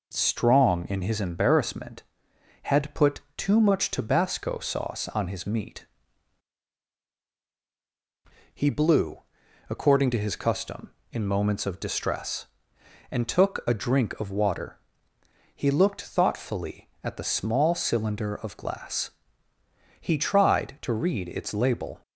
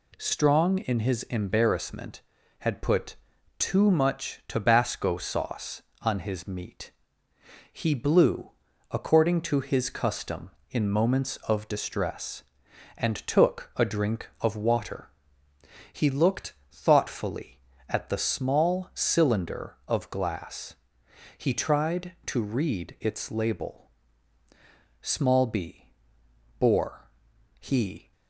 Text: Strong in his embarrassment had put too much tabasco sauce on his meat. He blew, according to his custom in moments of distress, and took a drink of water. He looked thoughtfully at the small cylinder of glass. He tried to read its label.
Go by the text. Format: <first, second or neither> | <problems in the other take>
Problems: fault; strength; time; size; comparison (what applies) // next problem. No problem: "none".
first | pauses between "put" and "too"; at 3.1 s; 0.42 s long; slight in the first // pauses between "looked" and "thoughtfully"; slight; at 16.5 s; 0.18 s long // goes on to say "Small b bore he"; strong; from 25.0 s on; 3.1 s long